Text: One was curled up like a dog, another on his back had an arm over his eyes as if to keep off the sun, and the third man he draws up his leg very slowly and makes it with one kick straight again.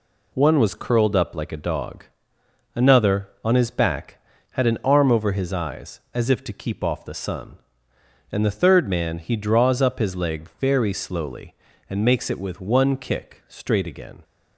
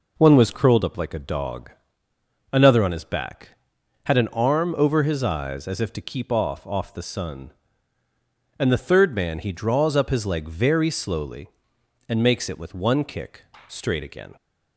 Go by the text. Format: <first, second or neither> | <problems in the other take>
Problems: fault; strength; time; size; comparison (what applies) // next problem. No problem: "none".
first | says "off" twice; at 6.6 s // pauses between "kick" and "straight"; slight; at 13.4 s; 0.24 s long